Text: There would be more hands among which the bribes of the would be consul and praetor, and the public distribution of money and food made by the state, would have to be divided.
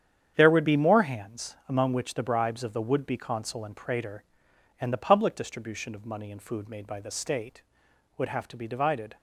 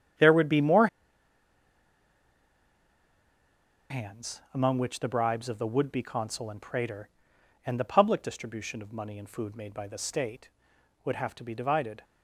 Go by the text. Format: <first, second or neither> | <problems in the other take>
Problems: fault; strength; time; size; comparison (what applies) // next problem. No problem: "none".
first | starts louder than the rest; strong; until 4.2 s; 8.5 dB; strong in the first // pauses between "more" and "hands"; strong; at 0.8 s; 3.0 s long